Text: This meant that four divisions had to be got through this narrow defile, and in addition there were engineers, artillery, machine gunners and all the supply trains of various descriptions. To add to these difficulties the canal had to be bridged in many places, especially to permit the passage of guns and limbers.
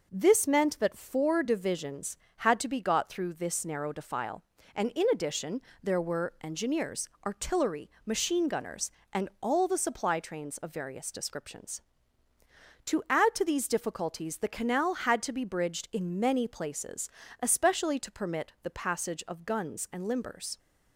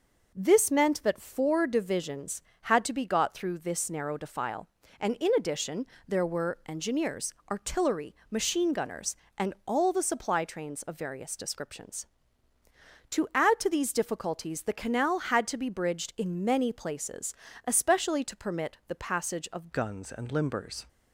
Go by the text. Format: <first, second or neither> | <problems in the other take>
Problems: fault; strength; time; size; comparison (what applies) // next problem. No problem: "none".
first | pauses between "addition" and "there"; slight; at 5.8 s; 0.22 s long; slight in the first // changes voice at "guns"; from 19.7 s on; 1.1 s long